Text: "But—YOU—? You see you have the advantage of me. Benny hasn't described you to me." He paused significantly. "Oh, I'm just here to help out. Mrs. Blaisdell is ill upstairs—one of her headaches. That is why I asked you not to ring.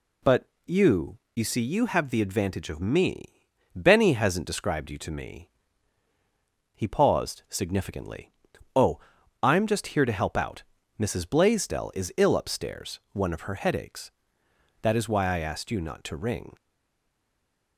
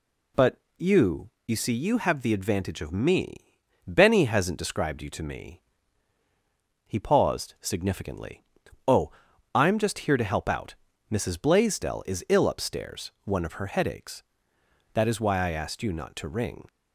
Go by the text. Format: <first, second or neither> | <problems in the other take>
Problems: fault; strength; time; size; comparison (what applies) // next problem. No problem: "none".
second | stays silent after the last word; noticeable; from 16.5 s on; 1.2 s long